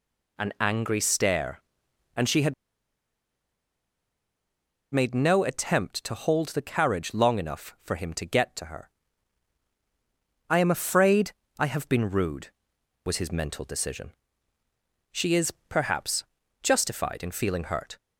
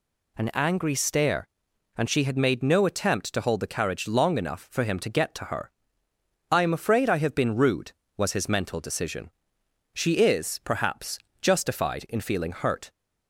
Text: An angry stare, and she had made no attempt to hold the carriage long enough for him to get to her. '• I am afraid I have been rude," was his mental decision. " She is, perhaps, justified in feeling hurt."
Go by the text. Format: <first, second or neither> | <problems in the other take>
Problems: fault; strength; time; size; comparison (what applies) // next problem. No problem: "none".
second | pauses between "had" and "made"; strong; at 2.5 s; 2.4 s long // pauses between "afraid" and "I"; slight; at 11.3 s; 0.26 s long